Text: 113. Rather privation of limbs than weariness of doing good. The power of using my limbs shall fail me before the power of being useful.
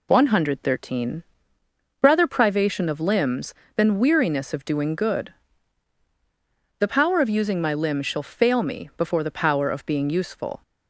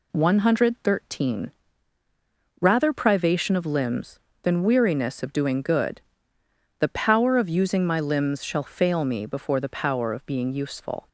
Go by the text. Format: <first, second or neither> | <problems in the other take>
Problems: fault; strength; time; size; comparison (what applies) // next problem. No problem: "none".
neither | none